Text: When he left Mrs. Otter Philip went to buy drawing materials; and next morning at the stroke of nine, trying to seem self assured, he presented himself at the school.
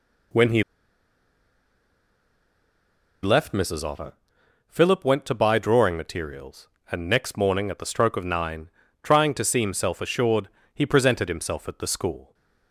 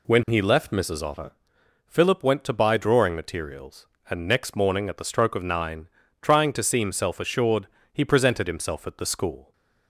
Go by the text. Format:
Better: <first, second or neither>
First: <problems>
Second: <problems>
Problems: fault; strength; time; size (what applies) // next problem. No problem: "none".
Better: second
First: pauses between "he" and "left"; strong; at 0.6 s; 2.6 s long // pauses between "Otter" and "Philip"; noticeable; at 4.1 s; 0.56 s long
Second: pauses between "Otter" and "Philip"; noticeable; at 1.3 s; 0.56 s long